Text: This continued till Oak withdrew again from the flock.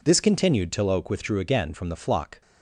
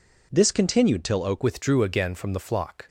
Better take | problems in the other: first | changes voice at "withdrew"; from 1.4 s on; 1.4 s long

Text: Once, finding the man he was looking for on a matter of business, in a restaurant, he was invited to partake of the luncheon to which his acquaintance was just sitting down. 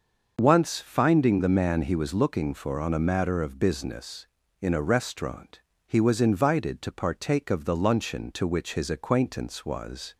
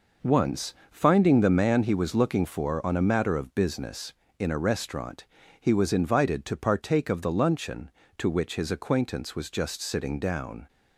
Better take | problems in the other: second | starts louder than the rest; until 1.4 s; 6 dB // stops before "just sitting down"; at 10.1 s

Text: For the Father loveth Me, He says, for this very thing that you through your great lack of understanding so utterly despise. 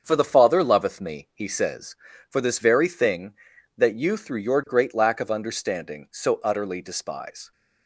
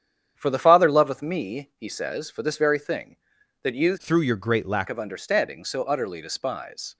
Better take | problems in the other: first | starts louder than the rest; strong; until 1.3 s; 9 dB; strong in the first // changes voice from "through" to "lack"; from 3.9 to 4.8 s; 0.9 s long

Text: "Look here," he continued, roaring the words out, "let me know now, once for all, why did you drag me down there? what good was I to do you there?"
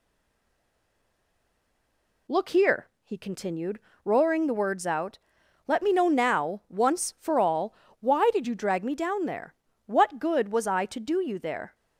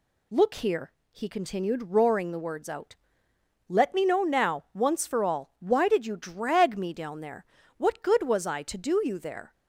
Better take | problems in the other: second | stays silent before the first word; until 2.2 s; 2.2 s long

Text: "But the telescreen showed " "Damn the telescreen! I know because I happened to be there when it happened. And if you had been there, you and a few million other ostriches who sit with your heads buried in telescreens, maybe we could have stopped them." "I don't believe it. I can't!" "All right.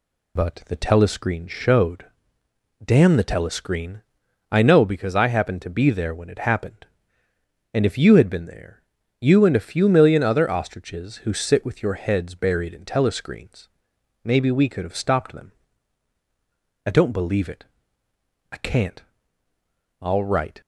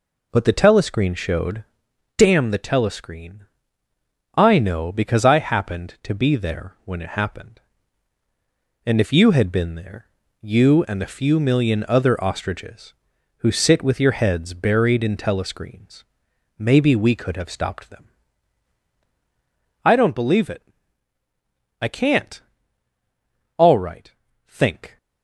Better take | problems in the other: first | goes on to say "Think"; from 24.4 s on; 0.50 s long

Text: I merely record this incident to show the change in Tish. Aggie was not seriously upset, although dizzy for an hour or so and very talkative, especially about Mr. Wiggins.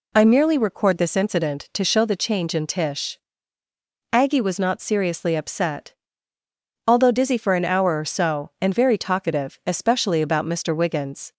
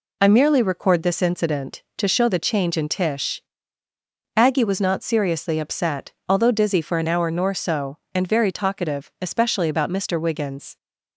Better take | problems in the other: first | says "nor" for "or"; at 7.3 s

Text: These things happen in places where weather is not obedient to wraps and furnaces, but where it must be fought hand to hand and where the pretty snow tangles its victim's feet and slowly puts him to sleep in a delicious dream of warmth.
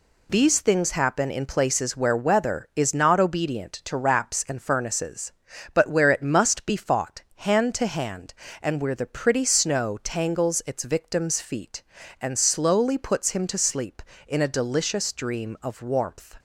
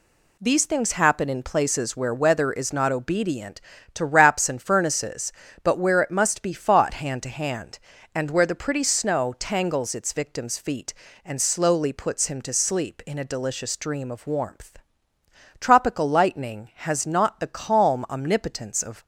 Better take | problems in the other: first | goes on to say "Tropical lightning has not the calm omnipotence of"; strong; from 15.5 s on; 3.4 s long

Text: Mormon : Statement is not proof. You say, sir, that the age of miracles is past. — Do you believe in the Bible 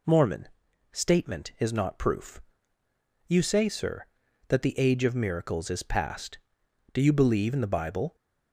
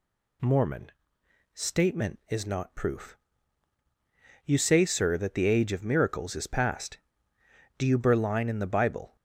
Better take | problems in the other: first | says "berline" for "believe"; at 7.9 s

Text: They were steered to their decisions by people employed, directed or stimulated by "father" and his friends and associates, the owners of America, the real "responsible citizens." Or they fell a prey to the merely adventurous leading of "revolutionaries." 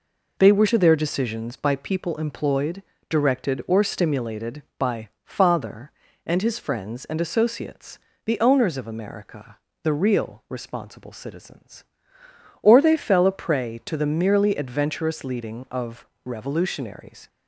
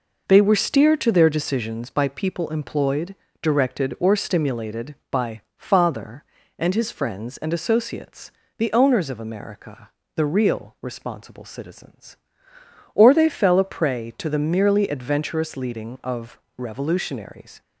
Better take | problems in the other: second | skips "steered"; at 0.6 s // pauses between "of" and "revolutionaries"; slight; at 16.0 s; 0.18 s long; slight in the second

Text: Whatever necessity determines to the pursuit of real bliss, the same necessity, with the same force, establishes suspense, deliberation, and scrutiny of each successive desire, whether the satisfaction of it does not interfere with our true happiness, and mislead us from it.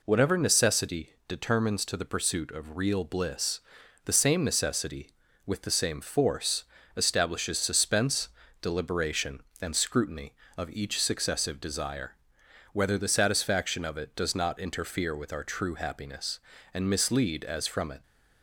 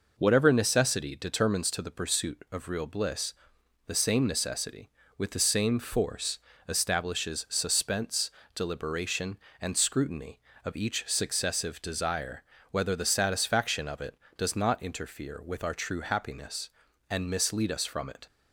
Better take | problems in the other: second | pauses between "necessity" and "determines"; slight; at 1.1 s; 0.16 s long // says "as" for "us"; at 17.4 s

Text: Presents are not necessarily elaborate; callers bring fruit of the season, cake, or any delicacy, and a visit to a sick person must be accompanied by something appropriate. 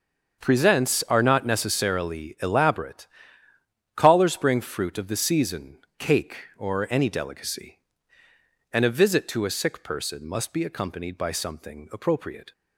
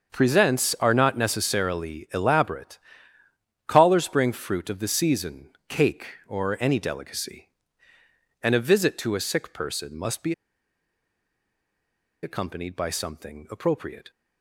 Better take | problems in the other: first | starts louder than the rest; until 1.1 s; 6.5 dB; also in the first // pauses between "be" and "accompanied"; strong; at 10.3 s; 1.8 s long

